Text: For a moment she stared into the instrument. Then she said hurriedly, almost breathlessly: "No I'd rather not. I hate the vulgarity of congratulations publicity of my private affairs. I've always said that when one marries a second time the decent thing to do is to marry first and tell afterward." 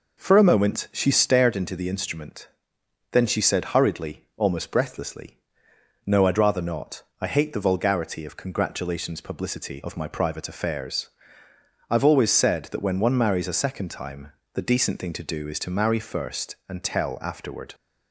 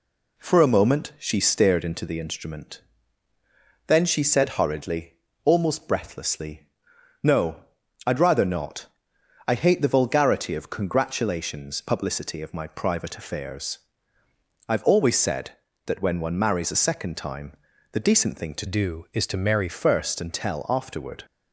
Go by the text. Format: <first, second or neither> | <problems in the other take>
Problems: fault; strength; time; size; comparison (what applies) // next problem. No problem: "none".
first | pauses between "No" and "I'd"; at 7.6 s; 0.42 s long // pauses between "time" and "the"; at 17.5 s; 0.38 s long; slight in the first // changes voice from "do" to "marry"; from 18.6 to 19.6 s; 1.0 s long